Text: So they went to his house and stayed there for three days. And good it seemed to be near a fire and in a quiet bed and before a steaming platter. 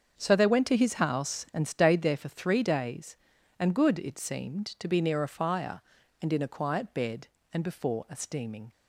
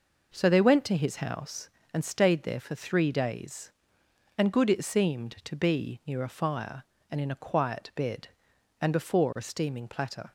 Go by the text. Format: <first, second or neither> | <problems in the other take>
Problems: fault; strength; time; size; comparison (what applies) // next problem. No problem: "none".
second | starts louder than the rest; until 1.2 s; 7 dB // stops before "platter"; at 8.7 s